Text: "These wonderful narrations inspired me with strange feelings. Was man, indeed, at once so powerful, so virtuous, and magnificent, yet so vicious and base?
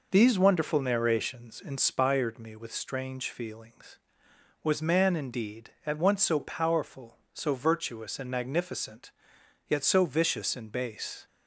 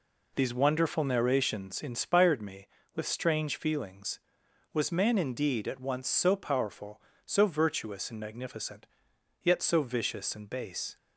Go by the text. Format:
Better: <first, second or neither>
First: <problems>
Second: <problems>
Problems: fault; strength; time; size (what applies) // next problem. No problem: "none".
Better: neither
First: none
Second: none